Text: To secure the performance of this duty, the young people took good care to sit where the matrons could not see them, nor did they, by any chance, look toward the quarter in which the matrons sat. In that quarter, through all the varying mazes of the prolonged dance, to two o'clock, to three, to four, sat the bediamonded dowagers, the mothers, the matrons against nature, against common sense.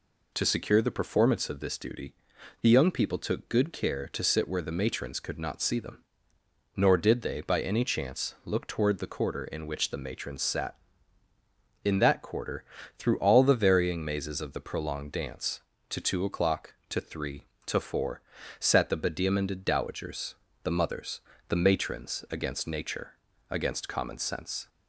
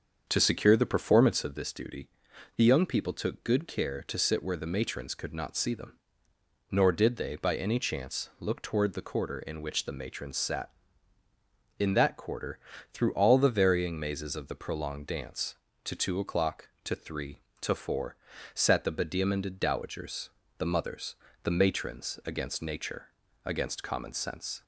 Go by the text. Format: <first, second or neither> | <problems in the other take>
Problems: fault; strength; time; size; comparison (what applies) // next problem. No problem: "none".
first | starts louder than the rest; until 1.6 s; 7 dB